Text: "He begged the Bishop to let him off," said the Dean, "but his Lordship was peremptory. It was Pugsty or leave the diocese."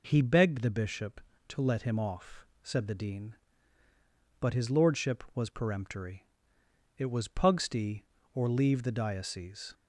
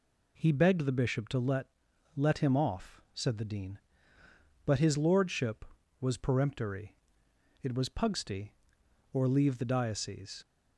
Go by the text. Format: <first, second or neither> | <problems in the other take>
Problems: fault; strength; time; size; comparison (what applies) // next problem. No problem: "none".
first | says "let" twice; at 2.1 s